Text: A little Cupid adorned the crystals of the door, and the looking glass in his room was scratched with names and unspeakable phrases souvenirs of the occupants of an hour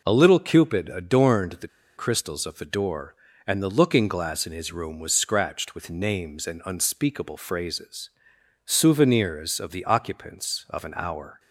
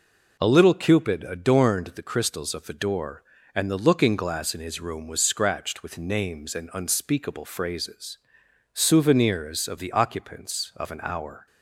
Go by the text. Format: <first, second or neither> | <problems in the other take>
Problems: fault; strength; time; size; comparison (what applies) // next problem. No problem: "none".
second | pauses between "the" and "crystals"; slight; at 1.6 s; 0.29 s long // pauses between "phrases" and "souvenirs"; noticeable; at 8.0 s; 0.58 s long; noticeable in the second